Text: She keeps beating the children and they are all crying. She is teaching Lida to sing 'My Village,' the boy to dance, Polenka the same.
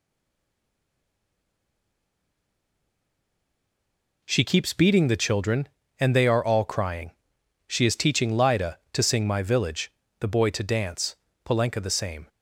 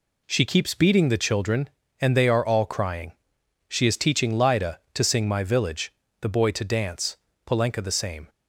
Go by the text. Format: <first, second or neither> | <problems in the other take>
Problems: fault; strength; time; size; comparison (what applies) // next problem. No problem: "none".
second | stays silent before the first word; strong; until 4.2 s; 4.2 s long